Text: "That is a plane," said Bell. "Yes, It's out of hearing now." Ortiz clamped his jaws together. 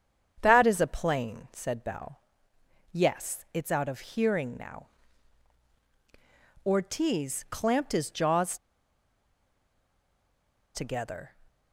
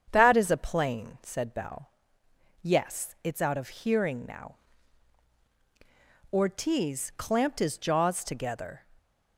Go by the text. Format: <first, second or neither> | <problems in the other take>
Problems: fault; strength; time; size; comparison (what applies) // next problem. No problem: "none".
second | starts louder than the rest; strong; until 1.4 s; 7.5 dB; strong in the second // pauses between "jaws" and "together"; strong; at 8.5 s; 2.1 s long